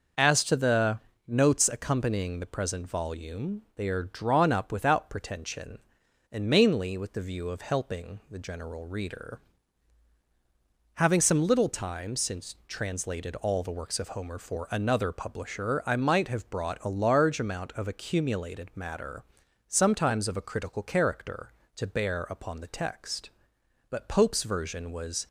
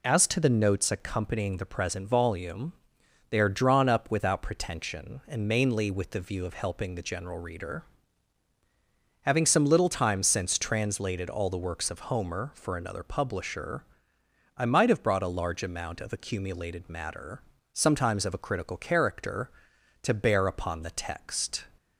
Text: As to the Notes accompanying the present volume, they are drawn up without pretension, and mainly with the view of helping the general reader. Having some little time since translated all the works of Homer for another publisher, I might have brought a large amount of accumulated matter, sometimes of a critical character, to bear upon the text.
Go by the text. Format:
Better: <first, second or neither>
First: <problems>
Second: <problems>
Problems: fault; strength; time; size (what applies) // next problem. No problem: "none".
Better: second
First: pauses between "the" and "Notes"; slight; at 0.9 s; 0.26 s long // goes on to say "But Pope's version was"; from 23.9 s on; 1.3 s long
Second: none